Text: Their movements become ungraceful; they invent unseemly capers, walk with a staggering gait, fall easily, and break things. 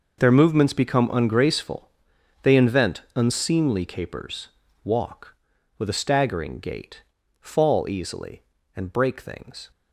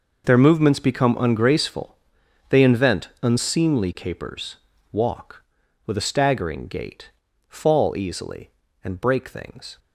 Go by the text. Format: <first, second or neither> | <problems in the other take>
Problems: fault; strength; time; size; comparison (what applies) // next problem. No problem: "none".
neither | none